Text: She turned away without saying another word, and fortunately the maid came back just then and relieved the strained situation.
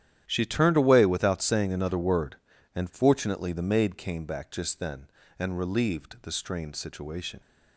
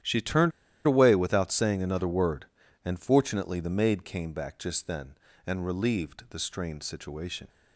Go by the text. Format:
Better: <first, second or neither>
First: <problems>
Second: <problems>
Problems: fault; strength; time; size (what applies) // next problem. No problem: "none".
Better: first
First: starts louder than the rest; strong; until 1.2 s; 11 dB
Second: starts louder than the rest; strong; until 1.3 s; 11 dB // pauses between "turned" and "away"; slight; at 0.5 s; 0.35 s long